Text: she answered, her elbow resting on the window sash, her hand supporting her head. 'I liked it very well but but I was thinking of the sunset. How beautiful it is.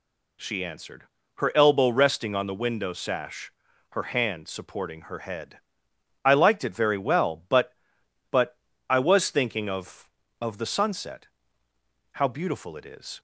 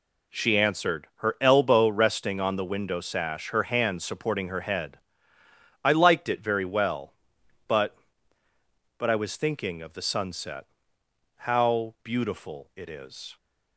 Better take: second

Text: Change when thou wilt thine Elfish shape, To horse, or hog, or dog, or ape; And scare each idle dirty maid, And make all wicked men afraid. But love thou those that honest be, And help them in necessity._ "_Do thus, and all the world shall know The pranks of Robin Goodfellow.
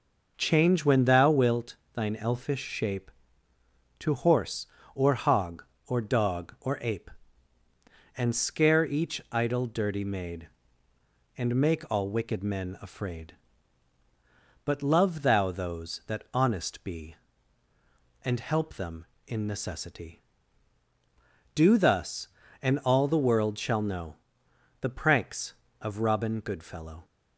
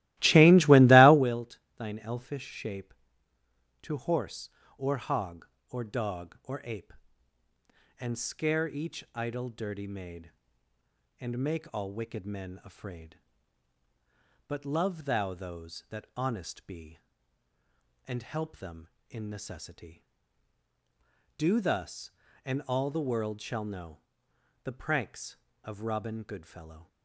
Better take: first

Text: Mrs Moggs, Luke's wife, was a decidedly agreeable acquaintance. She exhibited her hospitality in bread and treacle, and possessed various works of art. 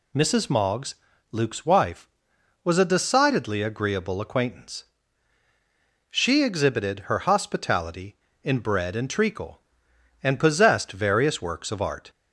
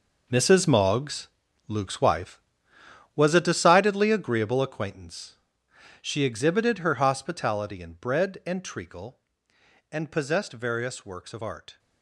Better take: first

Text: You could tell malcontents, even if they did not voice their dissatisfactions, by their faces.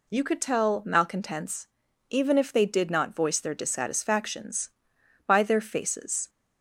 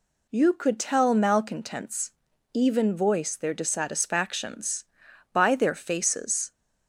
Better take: first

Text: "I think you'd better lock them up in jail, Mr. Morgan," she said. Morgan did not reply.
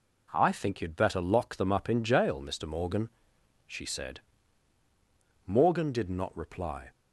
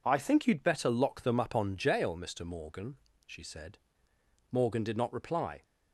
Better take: first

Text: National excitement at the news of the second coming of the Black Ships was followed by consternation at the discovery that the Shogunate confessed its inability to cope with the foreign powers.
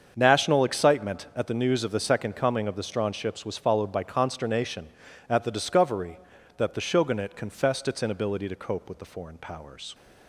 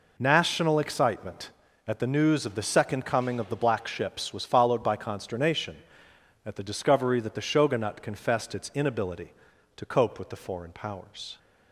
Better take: second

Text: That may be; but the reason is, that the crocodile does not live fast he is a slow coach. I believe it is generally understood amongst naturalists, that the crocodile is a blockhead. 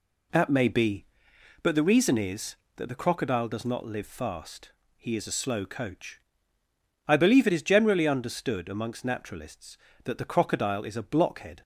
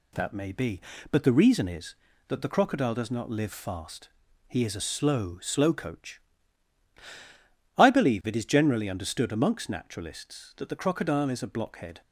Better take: first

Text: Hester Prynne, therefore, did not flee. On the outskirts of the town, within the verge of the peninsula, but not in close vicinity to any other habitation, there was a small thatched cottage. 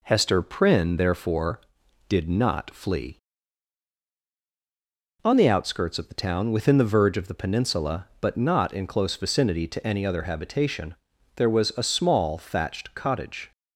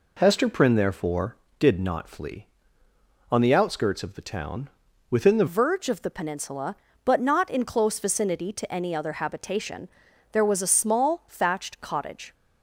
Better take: first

